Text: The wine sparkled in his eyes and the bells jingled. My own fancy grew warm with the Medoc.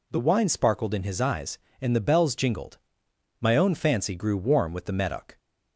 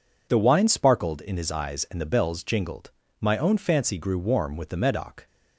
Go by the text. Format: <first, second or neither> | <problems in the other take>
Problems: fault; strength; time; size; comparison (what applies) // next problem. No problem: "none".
neither | none